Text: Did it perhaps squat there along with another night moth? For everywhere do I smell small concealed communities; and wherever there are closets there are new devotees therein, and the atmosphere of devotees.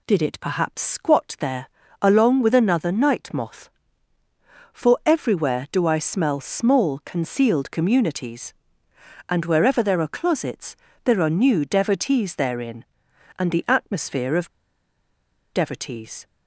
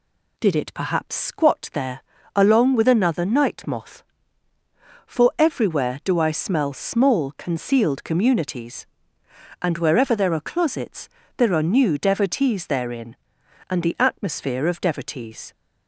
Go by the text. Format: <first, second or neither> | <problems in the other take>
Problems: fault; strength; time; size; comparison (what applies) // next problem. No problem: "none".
second | pauses between "there" and "along"; slight; at 1.6 s; 0.32 s long; slight in the second // pauses between "closets" and "there"; slight; at 10.7 s; 0.30 s long; slight in the second // pauses between "of" and "devotees"; at 14.4 s; 1.0 s long